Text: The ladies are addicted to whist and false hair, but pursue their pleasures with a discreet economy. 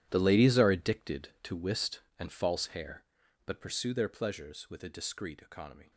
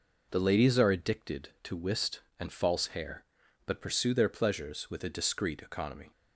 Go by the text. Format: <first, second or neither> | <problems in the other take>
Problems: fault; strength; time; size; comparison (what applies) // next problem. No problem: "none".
second | gets quieter; strong; throughout; 16 dB